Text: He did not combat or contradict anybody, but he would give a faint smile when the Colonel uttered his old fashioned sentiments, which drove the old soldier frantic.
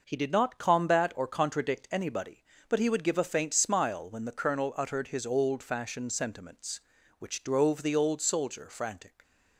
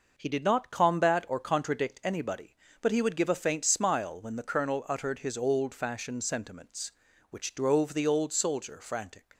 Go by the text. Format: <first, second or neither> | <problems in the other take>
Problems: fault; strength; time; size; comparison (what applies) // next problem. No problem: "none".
neither | none